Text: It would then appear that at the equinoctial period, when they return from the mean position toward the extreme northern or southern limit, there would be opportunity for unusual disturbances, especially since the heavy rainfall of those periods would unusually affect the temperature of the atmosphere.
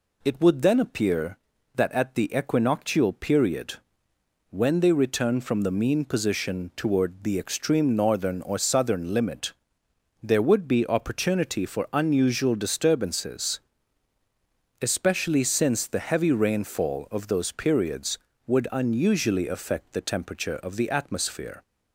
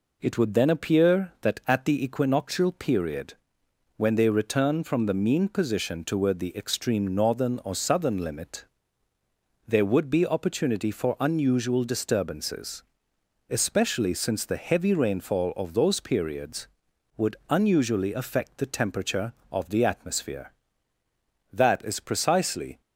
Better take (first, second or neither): first